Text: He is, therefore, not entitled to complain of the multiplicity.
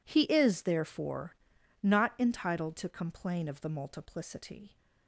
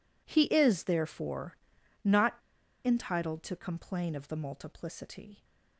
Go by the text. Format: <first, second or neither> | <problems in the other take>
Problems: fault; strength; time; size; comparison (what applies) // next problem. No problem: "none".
first | pauses between "not" and "entitled"; noticeable; at 2.3 s; 0.48 s long